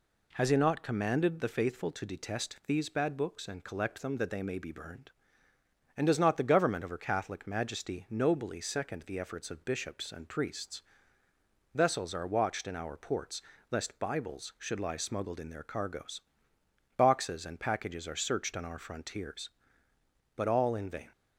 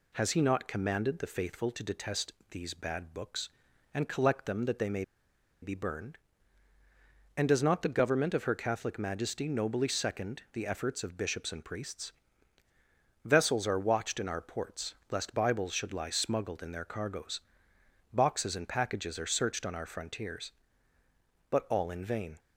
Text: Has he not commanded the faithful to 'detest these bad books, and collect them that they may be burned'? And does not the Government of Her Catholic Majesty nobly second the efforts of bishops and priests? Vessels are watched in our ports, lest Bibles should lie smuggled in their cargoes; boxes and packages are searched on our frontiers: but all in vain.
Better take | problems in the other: first | pauses between "detest" and "these"; slight; at 2.3 s; 0.18 s long // pauses between "may" and "be"; noticeable; at 5.0 s; 0.58 s long

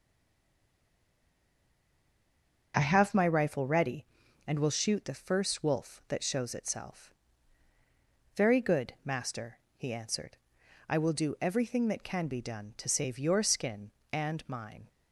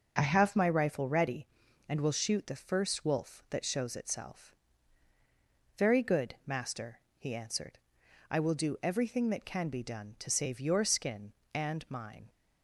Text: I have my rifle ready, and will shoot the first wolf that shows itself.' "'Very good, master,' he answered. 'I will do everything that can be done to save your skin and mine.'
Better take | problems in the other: second | stays silent before the first word; strong; until 2.7 s; 2.7 s long

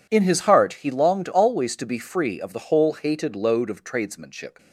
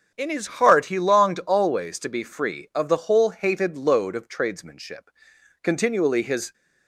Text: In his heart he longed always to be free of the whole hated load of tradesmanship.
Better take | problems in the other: first | starts louder than the rest; strong; until 1.2 s; 8.5 dB // goes on to say "Continually his"; noticeable; from 5.6 s on; 0.90 s long

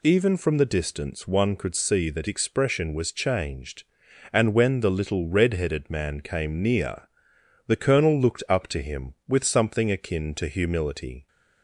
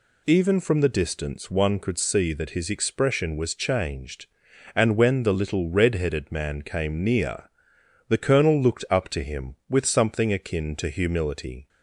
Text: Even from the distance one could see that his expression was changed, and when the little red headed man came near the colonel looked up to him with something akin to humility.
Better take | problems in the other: second | skips "his"; at 2.2 s // pauses between "near" and "the"; noticeable; at 7.0 s; 0.64 s long; noticeable in the second

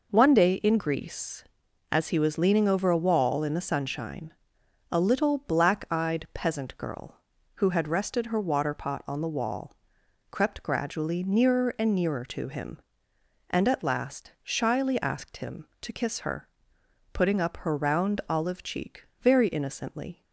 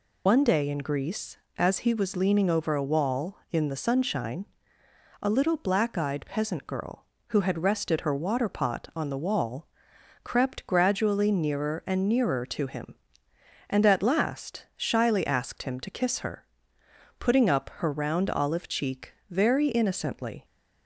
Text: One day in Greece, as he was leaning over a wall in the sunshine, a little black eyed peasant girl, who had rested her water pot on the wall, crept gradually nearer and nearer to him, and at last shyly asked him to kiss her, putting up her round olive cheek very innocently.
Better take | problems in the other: first | loses the start of "One"; at 0.2 s; 70 ms // pauses between "cheek" and "very"; slight; at 19.1 s; 0.16 s long; slight in the first

